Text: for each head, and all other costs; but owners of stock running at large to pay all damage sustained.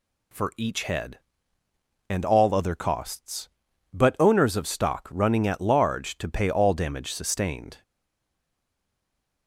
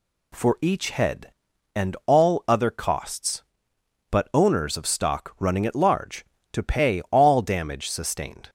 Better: second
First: stays silent after the last word; noticeable; from 7.8 s on; 1.6 s long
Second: none

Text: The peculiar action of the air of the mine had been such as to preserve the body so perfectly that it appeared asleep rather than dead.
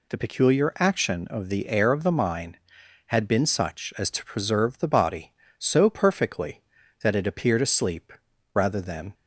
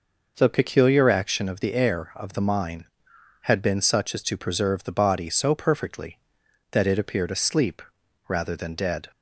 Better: second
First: pauses between "asleep" and "rather"; at 8.1 s; 0.42 s long // stops before "dead"; at 9.1 s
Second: pauses between "asleep" and "rather"; noticeable; at 7.8 s; 0.46 s long

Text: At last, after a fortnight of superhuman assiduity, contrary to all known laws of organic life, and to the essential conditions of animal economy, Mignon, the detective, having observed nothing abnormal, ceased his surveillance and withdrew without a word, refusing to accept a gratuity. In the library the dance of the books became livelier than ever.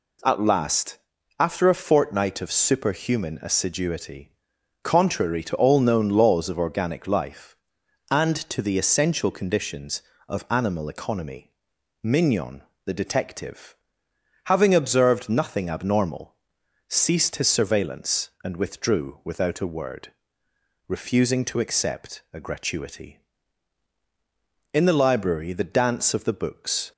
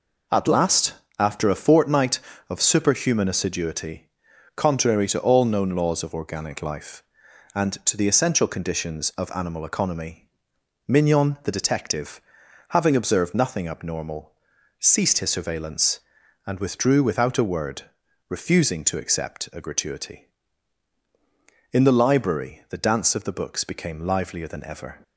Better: second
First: stops before "became livelier than ever"; at 26.9 s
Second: none

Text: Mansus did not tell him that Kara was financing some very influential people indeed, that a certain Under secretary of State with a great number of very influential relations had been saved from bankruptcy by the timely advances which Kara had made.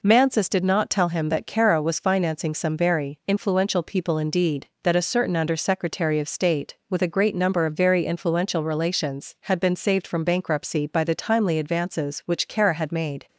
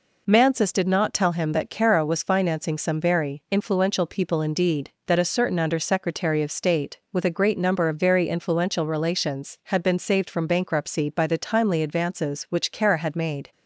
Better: neither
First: none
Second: none

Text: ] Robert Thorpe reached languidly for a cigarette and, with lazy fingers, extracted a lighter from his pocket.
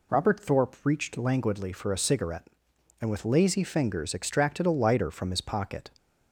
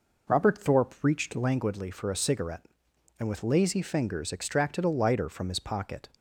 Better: first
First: none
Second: starts louder than the rest; noticeable; until 1.6 s; 4.5 dB

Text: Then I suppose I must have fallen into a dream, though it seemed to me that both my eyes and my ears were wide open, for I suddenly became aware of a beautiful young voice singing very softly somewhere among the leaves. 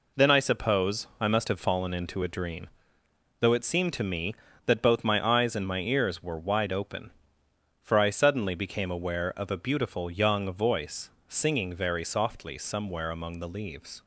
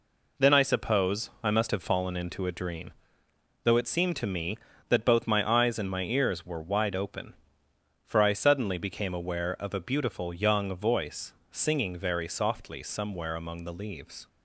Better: neither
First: pauses between "voice" and "singing"; slight; at 11.0 s; 0.20 s long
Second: pauses between "voice" and "singing"; slight; at 11.3 s; 0.20 s long

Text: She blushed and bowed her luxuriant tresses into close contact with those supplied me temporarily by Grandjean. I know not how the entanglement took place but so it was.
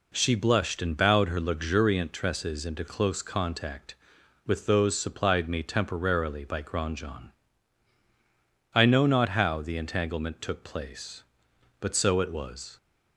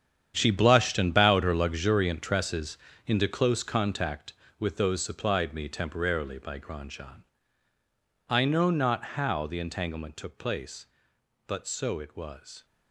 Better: first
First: none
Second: gets quieter; strong; throughout; 13.5 dB // pauses between "tresses" and "into"; slight; at 2.7 s; 0.30 s long

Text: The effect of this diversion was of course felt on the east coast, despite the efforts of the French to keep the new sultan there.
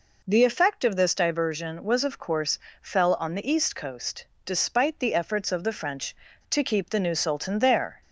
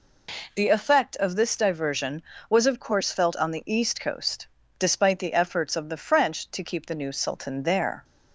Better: second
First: says "fell" for "felt"; at 2.8 s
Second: none

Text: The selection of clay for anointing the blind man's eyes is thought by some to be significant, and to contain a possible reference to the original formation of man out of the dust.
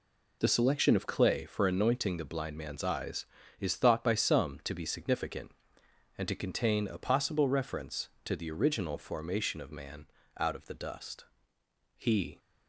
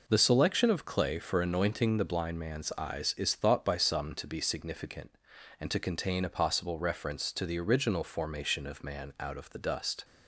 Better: second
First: pauses between "man" and "out"; slight; at 10.0 s; 0.30 s long // goes on to say "He"; slight; from 11.9 s on; 0.42 s long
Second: none

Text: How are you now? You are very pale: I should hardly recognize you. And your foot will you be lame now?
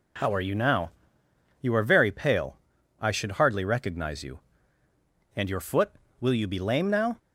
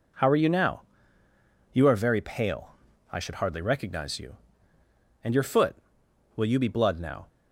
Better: first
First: none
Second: says "blood" for "lame"; at 6.6 s

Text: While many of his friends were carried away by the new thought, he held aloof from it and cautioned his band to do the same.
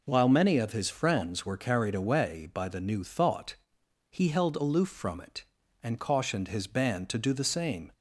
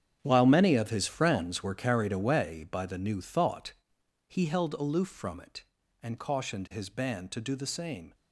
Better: first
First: none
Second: gets quieter; strong; throughout; 13 dB

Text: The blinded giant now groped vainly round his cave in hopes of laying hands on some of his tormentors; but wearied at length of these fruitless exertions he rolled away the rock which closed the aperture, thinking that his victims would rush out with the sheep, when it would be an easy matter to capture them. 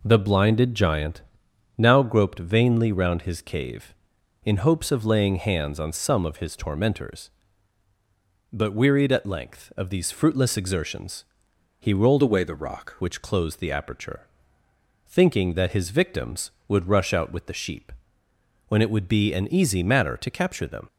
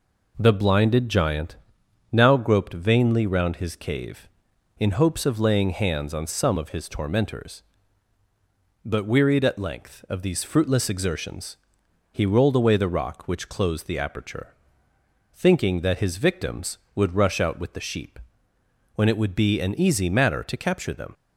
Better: second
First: pauses between "giant" and "now"; noticeable; at 1.2 s; 0.56 s long // pauses between "exertions" and "he"; noticeable; at 11.2 s; 0.54 s long // changes voice from "away" to "rock"; from 12.2 to 12.9 s; 0.7 s long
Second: pauses between "giant" and "now"; noticeable; at 1.5 s; 0.56 s long // pauses between "exertions" and "he"; noticeable; at 11.5 s; 0.54 s long

